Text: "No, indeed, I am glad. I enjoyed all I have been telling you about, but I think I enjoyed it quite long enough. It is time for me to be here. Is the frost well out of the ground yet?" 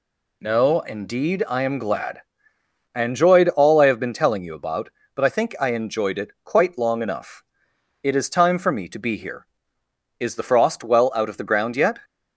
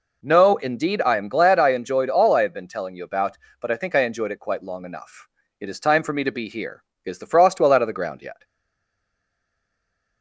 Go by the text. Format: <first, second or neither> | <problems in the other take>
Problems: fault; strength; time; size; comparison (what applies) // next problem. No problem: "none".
first | stays silent after the last word; noticeable; from 8.4 s on; 1.8 s long